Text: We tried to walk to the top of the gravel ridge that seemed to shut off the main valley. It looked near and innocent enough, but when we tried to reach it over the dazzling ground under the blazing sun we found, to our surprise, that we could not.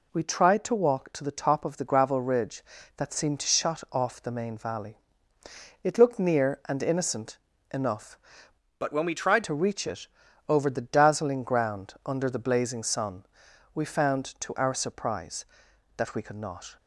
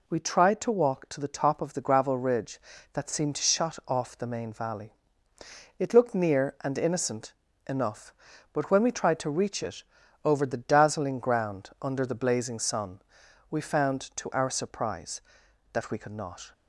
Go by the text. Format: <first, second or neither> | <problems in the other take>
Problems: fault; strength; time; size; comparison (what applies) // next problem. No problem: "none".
second | pauses between "innocent" and "enough"; slight; at 7.3 s; 0.32 s long; slight in the second // changes voice from "but" to "tried"; from 8.7 to 9.4 s; 0.7 s long // pauses between "it" and "over"; at 10.0 s; 0.40 s long; also in the second // pauses between "sun" and "we"; noticeable; at 13.2 s; 0.50 s long; noticeable in the second